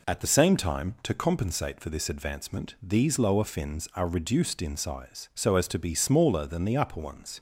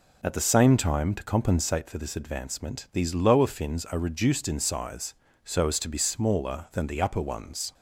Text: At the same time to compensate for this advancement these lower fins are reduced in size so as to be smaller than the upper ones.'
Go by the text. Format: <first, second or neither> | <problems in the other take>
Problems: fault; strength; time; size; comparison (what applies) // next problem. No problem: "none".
neither | none